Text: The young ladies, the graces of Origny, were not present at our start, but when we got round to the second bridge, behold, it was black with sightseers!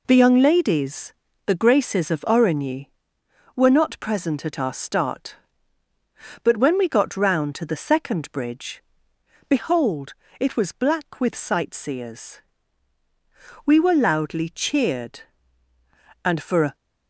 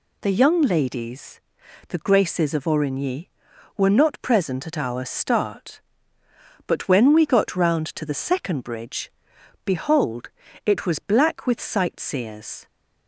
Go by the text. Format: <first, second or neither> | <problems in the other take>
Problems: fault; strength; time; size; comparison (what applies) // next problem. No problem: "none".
second | goes on to say "We were loudly cheered and for a"; strong; from 13.6 s on; 3.1 s long